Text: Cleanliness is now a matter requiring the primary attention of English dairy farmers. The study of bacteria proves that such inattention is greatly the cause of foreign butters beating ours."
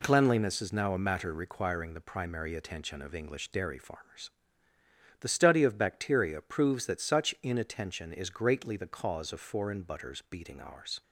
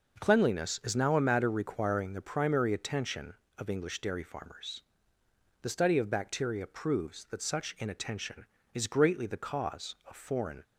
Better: first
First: none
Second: stops before "butters beating ours"; at 10.6 s

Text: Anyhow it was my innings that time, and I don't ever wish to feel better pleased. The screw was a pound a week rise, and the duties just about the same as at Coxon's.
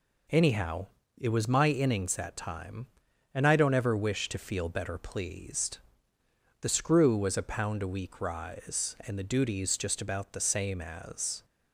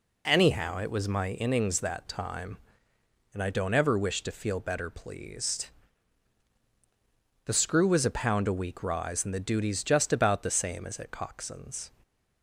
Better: second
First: pauses between "Anyhow" and "it"; slight; at 0.8 s; 0.30 s long // stops before "at Coxon's"; at 11.4 s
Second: none

